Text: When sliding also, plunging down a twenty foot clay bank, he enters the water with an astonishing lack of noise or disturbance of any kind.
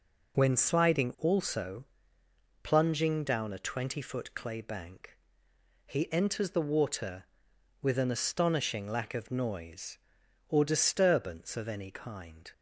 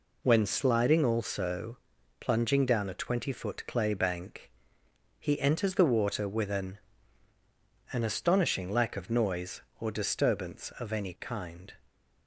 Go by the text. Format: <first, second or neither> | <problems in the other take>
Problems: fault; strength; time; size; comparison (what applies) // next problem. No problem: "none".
first | says "an" twice; at 7.9 s